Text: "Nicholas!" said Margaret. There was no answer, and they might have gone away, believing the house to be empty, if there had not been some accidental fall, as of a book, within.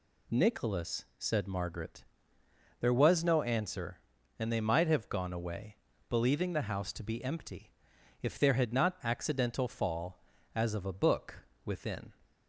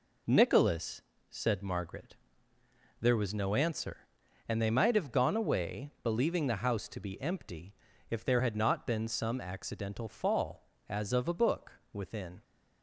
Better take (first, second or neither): second